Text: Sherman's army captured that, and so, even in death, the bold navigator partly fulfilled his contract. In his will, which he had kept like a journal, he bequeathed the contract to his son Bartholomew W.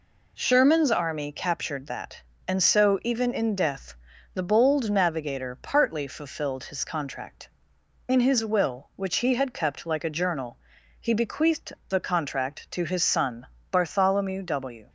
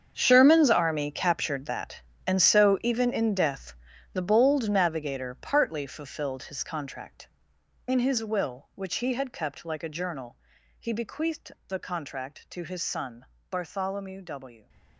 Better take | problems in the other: first | gets quieter; strong; throughout; 15.5 dB // pauses between "bequeathed" and "the"; slight; at 11.5 s; 0.16 s long; slight in the first // pauses between "son" and "Bartholomew"; slight; at 13.2 s; 0.26 s long; slight in the first

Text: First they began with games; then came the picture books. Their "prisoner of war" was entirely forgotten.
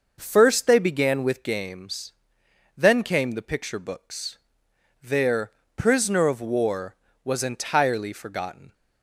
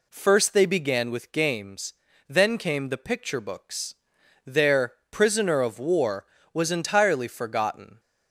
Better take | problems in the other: neither | pauses between "Their" and "prisoner"; slight; the same in both

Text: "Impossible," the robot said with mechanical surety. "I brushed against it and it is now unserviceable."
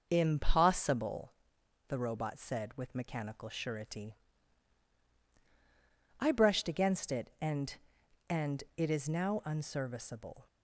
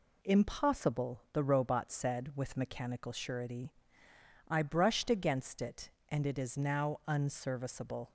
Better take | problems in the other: second | says "and" twice; at 8.2 s

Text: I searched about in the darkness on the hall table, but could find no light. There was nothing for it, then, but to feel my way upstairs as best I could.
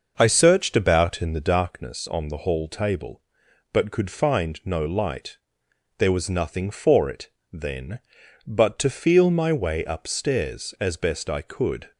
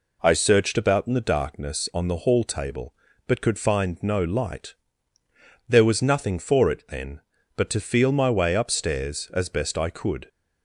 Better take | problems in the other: second | starts louder than the rest; noticeable; until 1.8 s; 6 dB

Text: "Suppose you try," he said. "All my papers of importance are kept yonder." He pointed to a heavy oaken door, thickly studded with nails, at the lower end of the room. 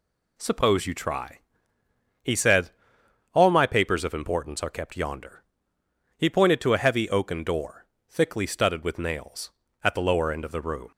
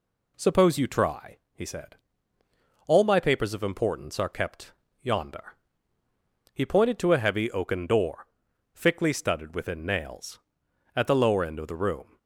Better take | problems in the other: first | pauses between "kept" and "yonder"; slight; at 4.7 s; 0.28 s long // says "within" for "with"; at 9.5 s

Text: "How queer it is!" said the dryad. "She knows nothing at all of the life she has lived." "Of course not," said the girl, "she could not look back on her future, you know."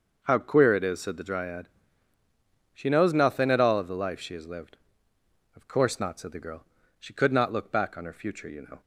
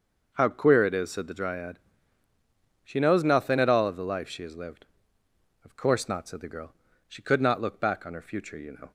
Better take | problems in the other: neither | none

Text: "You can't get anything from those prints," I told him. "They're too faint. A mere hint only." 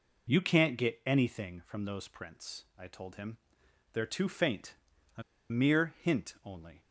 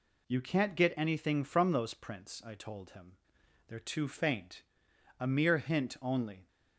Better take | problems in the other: second | pauses between "A" and "mere"; slight; at 5.2 s; 0.27 s long

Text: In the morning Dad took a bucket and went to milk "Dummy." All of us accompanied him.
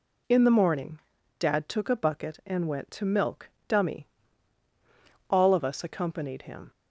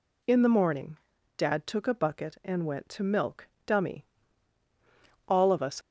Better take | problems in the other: first | pauses between "morning" and "Dad"; at 0.9 s; 0.38 s long; also in the first // pauses between "milk" and "Dummy"; slight; at 3.4 s; 0.18 s long; slight in the first // stops before "accompanied him"; at 5.8 s

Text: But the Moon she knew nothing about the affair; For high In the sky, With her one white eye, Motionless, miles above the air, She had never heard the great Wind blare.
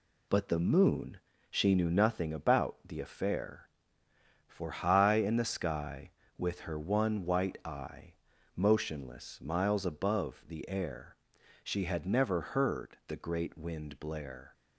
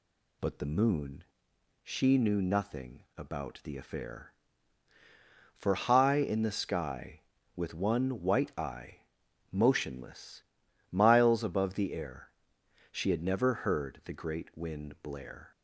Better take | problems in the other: first | pauses between "Moon" and "she"; noticeable; at 1.2 s; 0.58 s long; slight in the first // skips "her"; at 7.7 s

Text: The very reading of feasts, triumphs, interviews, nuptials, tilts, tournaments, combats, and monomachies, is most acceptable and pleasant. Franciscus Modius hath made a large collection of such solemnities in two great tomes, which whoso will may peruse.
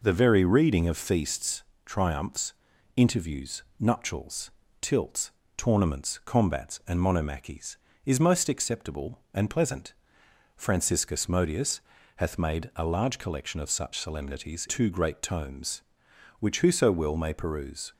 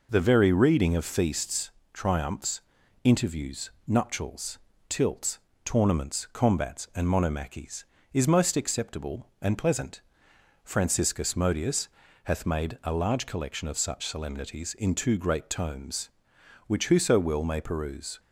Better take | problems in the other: second | pauses between "Modius" and "hath"; at 11.7 s; 0.38 s long; also in the second // skips "in"; at 14.6 s

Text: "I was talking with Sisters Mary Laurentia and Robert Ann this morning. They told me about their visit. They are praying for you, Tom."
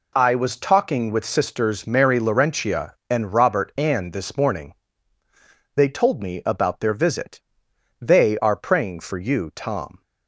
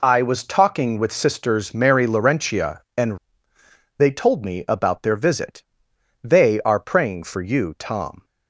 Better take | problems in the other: first | skips "Robert Ann this morning"; at 3.5 s

